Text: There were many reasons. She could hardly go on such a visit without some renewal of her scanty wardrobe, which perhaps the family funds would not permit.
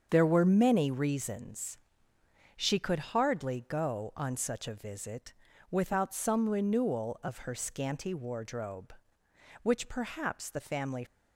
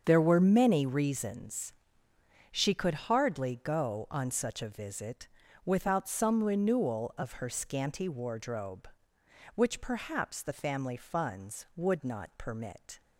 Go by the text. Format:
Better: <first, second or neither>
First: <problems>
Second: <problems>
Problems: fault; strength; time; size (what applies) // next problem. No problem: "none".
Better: second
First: starts louder than the rest; strong; until 1.1 s; 7 dB // pauses between "visit" and "without"; slight; at 5.3 s; 0.36 s long // stops before "funds would not permit"; at 11.0 s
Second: starts louder than the rest; strong; until 1.0 s; 7 dB // pauses between "visit" and "without"; slight; at 5.2 s; 0.36 s long